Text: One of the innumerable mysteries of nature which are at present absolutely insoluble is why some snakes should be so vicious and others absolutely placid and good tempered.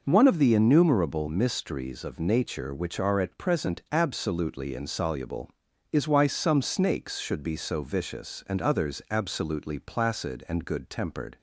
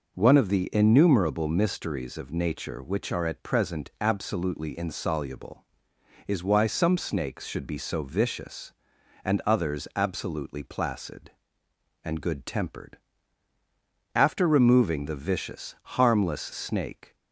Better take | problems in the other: first | goes on to say "After removing the vicious harmless snake"; strong; from 14.1 s on; 3.0 s long

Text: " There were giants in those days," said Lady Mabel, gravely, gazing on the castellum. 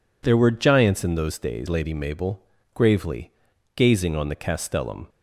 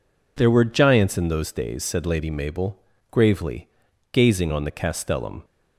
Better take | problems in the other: second | skips "said"; at 1.6 s

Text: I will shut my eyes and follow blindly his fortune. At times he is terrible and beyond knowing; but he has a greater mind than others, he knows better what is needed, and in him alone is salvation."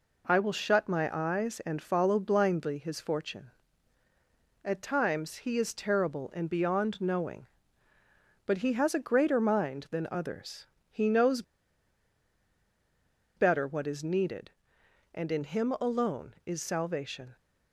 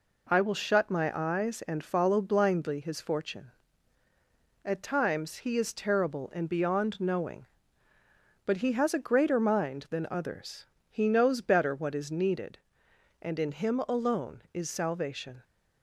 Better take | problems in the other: second | pauses between "knows" and "better"; strong; at 11.4 s; 1.9 s long

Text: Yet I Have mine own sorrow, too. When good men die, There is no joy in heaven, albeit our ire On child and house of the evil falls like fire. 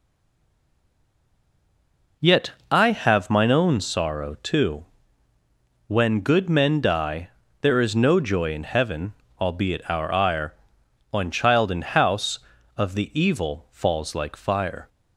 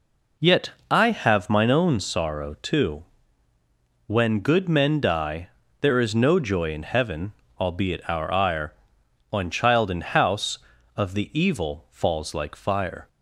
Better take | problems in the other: second | stays silent before the first word; until 2.2 s; 2.2 s long // pauses between "Yet" and "I"; slight; at 2.5 s; 0.18 s long; slight in the second

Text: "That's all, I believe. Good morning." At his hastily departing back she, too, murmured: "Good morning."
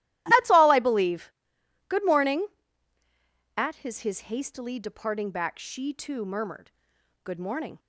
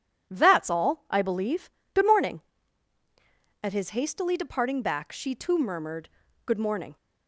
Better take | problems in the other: second | starts louder than the rest; strong; until 1.2 s; 14.5 dB // says "his" twice; at 4.0 s

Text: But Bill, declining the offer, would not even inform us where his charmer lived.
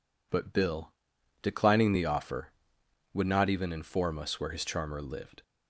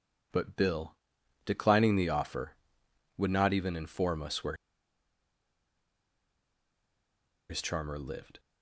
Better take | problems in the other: first | pauses between "where" and "his"; strong; at 4.5 s; 2.9 s long

